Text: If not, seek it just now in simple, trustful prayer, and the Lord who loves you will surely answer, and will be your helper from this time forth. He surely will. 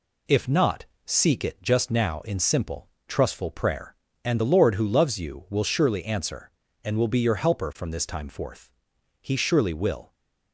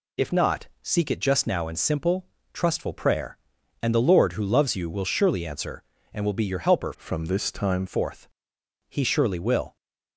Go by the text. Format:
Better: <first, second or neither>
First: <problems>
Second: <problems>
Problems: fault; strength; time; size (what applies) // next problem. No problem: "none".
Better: first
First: none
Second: changes voice from "from" to "time"; from 6.9 to 7.8 s; 0.9 s long